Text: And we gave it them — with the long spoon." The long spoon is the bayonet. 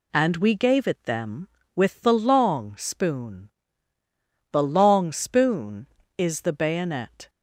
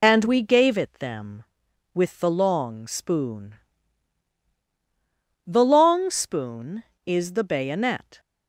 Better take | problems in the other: first | loses the start of "And"; at 0.0 s; 45 ms

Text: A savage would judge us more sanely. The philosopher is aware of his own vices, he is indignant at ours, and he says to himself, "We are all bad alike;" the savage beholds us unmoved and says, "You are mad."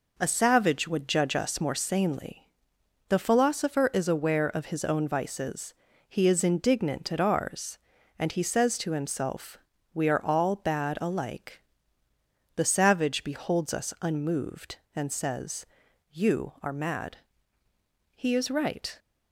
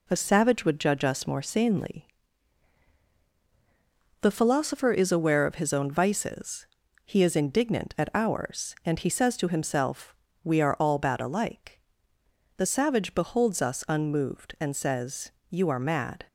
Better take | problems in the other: second | goes on to say "He is right"; noticeable; from 18.1 s on; 0.84 s long

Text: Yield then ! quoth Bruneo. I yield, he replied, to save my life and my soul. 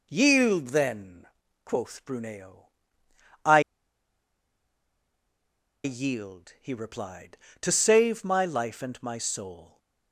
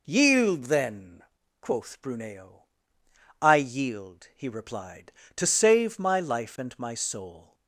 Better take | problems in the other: second | pauses between "I" and "yield"; strong; at 3.6 s; 2.2 s long

